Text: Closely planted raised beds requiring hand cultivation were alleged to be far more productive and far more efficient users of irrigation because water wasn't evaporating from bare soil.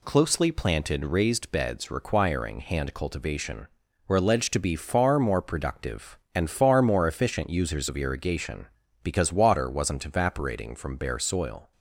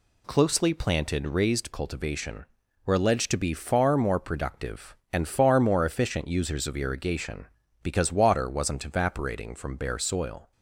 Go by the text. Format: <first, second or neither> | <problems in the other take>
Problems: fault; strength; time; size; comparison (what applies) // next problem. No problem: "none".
first | skips "beds requiring hand"; at 1.7 s